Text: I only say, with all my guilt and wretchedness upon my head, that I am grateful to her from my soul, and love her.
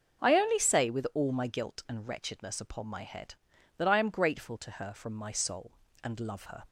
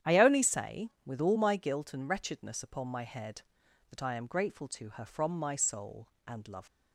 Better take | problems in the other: first | starts louder than the rest; strong; until 1.1 s; 10 dB; noticeable in the first // stops before "her"; at 6.6 s

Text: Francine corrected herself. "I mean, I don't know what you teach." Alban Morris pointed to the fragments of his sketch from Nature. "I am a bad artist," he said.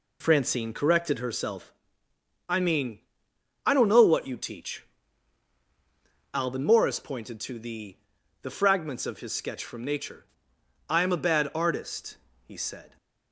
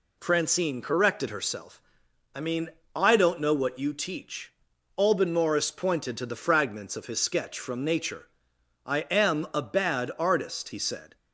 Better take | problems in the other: second | says "the" twice; at 8.4 s

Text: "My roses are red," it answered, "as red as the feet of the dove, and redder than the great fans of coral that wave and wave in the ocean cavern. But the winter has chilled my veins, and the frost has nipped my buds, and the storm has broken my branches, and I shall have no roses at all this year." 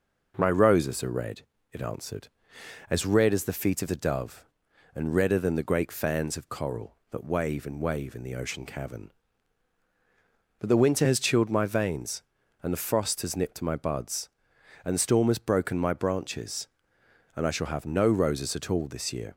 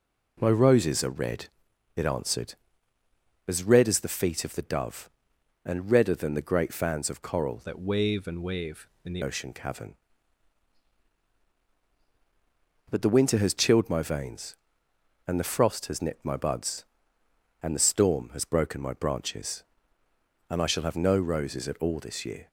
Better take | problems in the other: first | changes voice from "that" to "the"; from 7.6 to 9.2 s; 1.6 s long

